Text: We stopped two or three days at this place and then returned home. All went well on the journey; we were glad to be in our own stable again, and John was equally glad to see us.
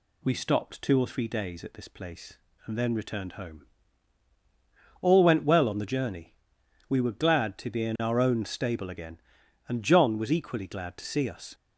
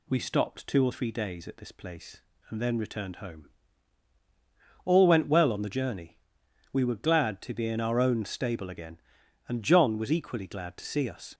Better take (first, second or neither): neither